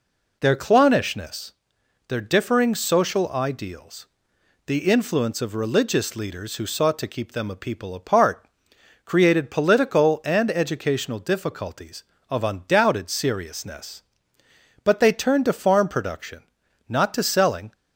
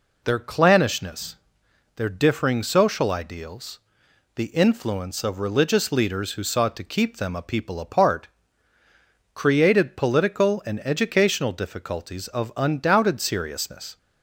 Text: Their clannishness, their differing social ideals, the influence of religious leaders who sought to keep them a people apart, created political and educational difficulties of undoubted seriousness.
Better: second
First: goes on to say "But they turned to farm production not to selling"; strong; from 14.8 s on; 2.9 s long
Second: none

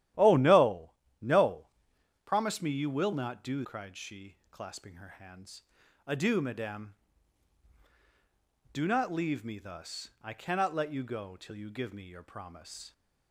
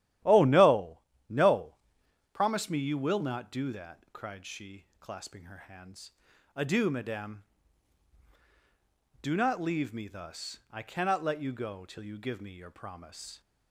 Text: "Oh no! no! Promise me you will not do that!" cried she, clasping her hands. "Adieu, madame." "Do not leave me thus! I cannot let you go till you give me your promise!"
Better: second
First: starts louder than the rest; strong; until 1.4 s; 12.5 dB // skips "that"; at 3.6 s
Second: starts louder than the rest; strong; until 1.5 s; 12.5 dB

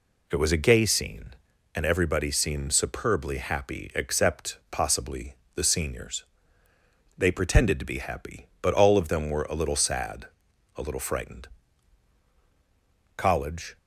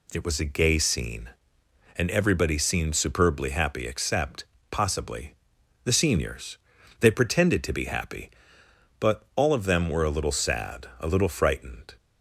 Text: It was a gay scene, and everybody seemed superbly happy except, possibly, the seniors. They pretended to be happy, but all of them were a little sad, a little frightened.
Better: second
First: goes on to say "College"; noticeable; from 13.1 s on; 0.62 s long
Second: none

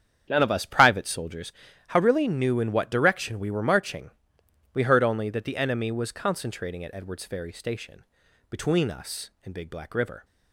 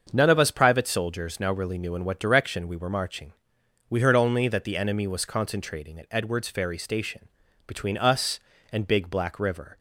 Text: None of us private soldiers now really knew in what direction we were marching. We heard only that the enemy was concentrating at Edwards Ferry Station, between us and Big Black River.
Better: second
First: starts louder than the rest; strong; until 1.2 s; 8 dB // says "how" for "now"; at 1.8 s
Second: starts louder than the rest; until 1.1 s; 6.5 dB

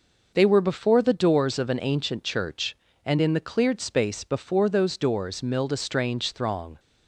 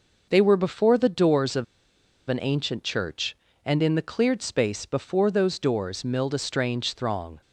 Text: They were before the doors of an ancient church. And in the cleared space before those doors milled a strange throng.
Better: first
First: none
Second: pauses between "of" and "an"; noticeable; at 1.6 s; 0.63 s long

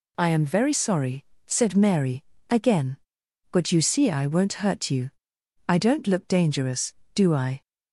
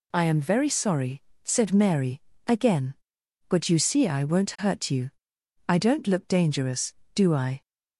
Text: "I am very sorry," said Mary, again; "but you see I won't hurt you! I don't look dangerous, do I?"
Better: neither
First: none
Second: none

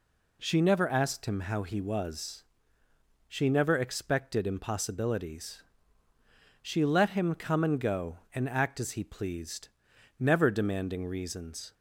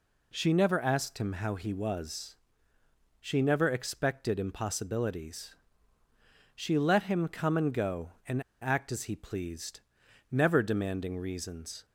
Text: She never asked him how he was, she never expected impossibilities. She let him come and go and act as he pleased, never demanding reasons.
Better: first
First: none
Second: pauses between "and" and "act"; slight; at 8.4 s; 0.21 s long

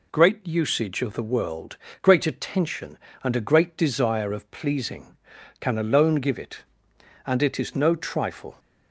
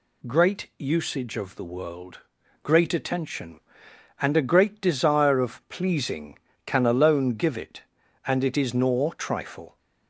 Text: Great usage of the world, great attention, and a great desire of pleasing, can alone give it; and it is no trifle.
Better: first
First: none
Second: says "nor" for "no"; at 8.7 s

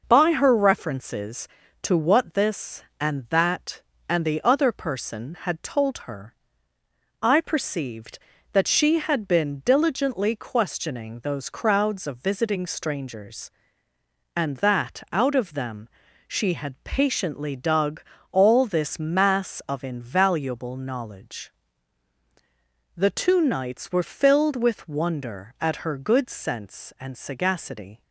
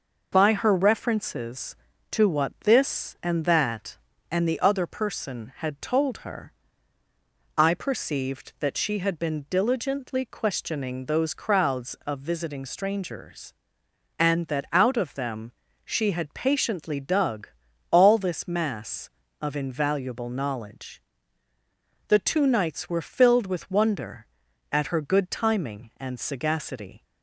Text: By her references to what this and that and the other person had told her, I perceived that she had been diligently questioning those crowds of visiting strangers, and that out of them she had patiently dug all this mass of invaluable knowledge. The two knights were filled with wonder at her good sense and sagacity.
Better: first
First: pauses between "them" and "she"; at 15.8 s; 0.38 s long // pauses between "dug" and "all"; slight; at 18.0 s; 0.30 s long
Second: pauses between "them" and "she"; slight; at 15.5 s; 0.34 s long // pauses between "dug" and "all"; at 17.4 s; 0.44 s long // says "timing" for "sense"; at 25.2 s

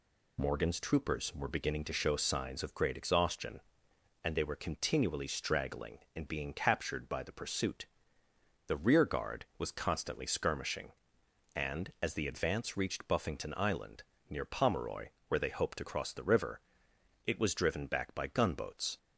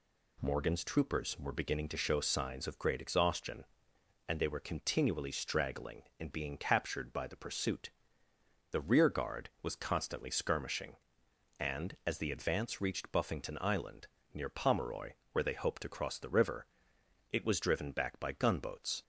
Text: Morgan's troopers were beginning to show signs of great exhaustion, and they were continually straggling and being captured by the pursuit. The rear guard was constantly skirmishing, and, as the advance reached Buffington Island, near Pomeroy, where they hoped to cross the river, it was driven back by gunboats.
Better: second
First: loses the start of "Morgan's"; at 0.3 s; 45 ms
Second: none

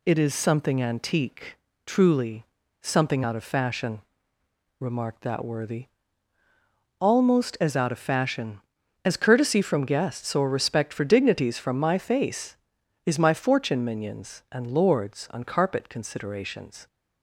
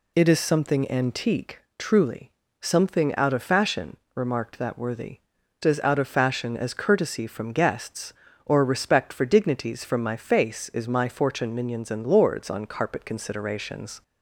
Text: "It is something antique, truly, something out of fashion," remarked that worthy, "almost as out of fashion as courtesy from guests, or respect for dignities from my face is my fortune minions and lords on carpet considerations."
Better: first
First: none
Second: skips "almost"; at 5.4 s

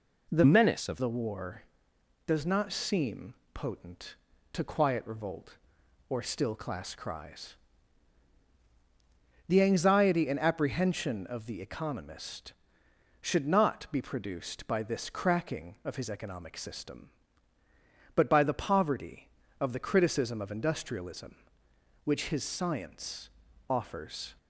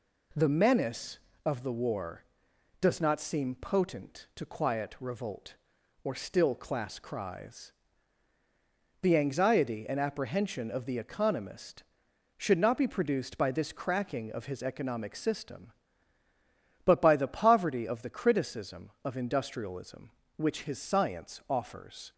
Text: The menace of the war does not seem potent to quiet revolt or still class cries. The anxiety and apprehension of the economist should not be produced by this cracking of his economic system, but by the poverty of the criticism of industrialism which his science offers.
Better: second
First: changes voice from "menace" to "of"; from 0.4 to 1.0 s; 0.6 s long // pauses between "seem" and "potent"; slight; at 3.3 s; 0.20 s long // pauses between "science" and "offers"; at 23.2 s; 0.40 s long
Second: none

